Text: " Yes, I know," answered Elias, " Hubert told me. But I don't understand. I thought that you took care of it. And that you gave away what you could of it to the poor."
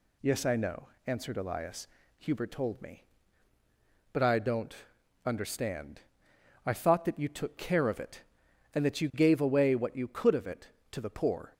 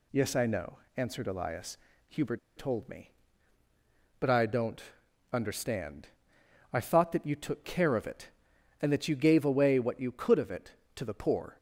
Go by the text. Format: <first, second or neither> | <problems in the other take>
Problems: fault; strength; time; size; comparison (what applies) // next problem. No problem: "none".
first | pauses between "Hubert" and "told"; slight; at 2.3 s; 0.19 s long // pauses between "don't" and "understand"; noticeable; at 4.8 s; 0.48 s long; noticeable in the first